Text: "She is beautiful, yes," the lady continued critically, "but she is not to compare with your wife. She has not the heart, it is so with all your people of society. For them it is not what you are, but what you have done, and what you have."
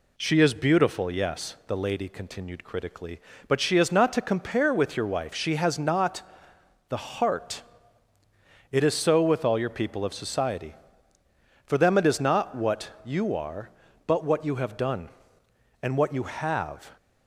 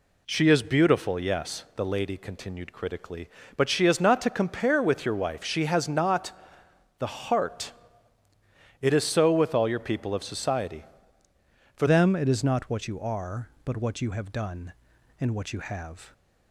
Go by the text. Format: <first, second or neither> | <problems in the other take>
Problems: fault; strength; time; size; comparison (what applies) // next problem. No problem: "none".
first | pauses between "not" and "the"; noticeable; at 6.3 s; 0.66 s long; noticeable in the first // changes voice at "them"; from 11.8 s on; 4.3 s long